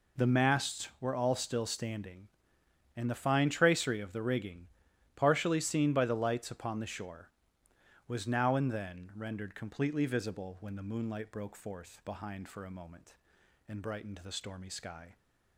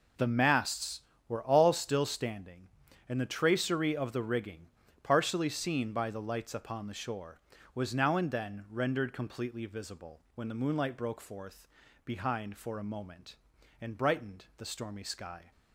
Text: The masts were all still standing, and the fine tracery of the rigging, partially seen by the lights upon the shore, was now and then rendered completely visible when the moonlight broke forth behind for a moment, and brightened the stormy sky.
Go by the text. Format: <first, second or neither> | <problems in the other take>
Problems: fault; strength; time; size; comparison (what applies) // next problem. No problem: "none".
first | skips "fine"; at 3.2 s // pauses between "forth" and "behind"; at 11.6 s; 0.40 s long